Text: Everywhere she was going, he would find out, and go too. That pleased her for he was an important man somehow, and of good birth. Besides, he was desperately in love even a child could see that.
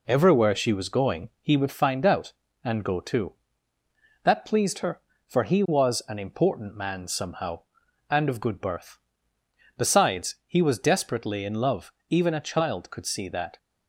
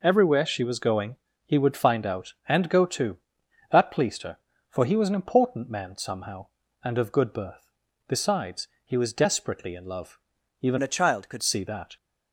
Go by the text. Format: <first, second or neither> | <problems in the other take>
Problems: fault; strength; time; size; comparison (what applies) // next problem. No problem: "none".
first | pauses between "love" and "even"; at 10.1 s; 0.44 s long; slight in the first // changes voice from "a" to "could"; from 10.8 to 11.4 s; 0.6 s long